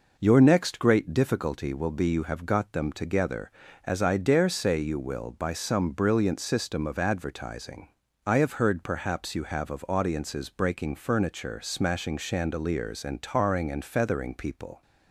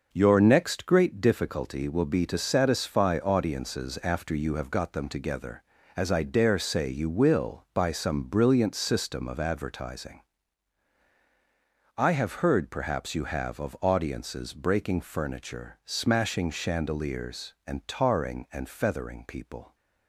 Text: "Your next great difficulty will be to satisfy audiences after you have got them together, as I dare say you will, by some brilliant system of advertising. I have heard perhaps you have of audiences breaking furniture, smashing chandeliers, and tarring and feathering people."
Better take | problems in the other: second | skips "to satisfy audiences after"; at 2.0 s

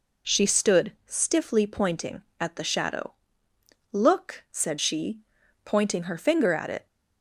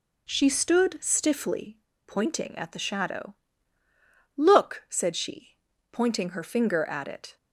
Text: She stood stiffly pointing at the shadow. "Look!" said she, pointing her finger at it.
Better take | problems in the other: first | pauses between "stiffly" and "pointing"; slight; at 1.7 s; 0.28 s long

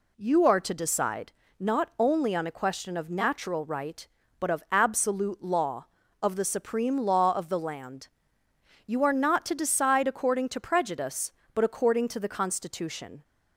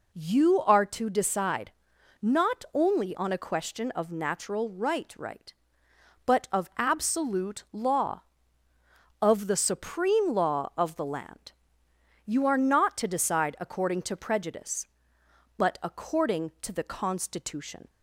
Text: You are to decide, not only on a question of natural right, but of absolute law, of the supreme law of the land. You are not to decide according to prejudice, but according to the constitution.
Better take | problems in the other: first | says "right" twice; at 5.1 s

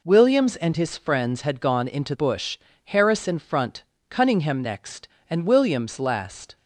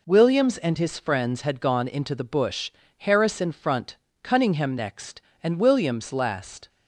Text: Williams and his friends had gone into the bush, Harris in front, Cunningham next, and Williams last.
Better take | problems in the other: second | skips "the"; at 2.1 s

